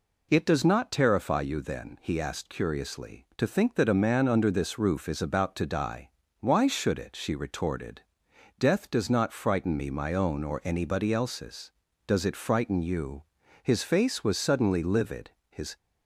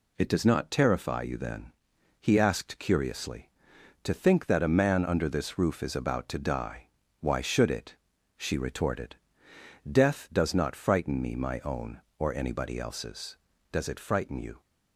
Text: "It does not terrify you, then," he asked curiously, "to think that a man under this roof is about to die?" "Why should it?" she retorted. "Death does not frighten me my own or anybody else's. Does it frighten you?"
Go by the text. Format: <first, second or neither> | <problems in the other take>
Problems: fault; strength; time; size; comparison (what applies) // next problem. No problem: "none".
second | goes on to say "His face was suddenly livid his"; strong; from 13.6 s on; 2.1 s long